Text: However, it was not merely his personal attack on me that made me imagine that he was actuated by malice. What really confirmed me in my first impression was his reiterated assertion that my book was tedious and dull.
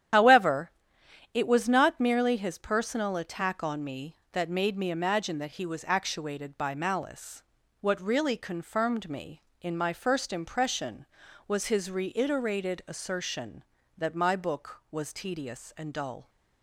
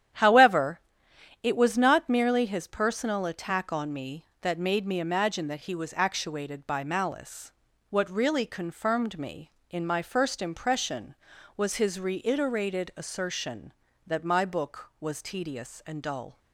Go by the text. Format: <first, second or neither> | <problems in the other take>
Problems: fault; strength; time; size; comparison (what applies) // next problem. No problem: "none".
second | loses the start of "However"; at 0.1 s; 70 ms // starts louder than the rest; strong; until 1.7 s; 10.5 dB; strong in the second